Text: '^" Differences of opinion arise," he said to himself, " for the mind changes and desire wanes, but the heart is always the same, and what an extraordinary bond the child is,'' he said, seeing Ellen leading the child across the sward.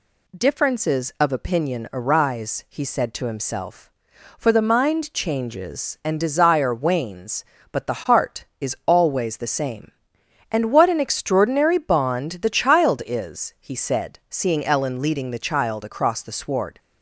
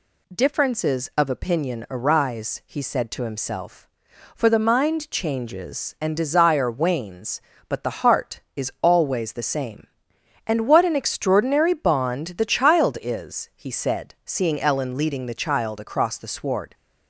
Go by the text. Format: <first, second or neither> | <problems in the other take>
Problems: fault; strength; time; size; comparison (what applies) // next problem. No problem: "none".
neither | none